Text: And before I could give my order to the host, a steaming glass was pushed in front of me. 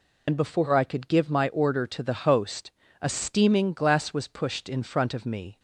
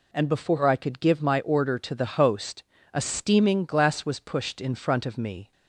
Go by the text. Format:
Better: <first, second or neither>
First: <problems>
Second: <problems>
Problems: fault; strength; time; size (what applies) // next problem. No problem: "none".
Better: second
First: loses the start of "And"; at 0.2 s; 65 ms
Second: none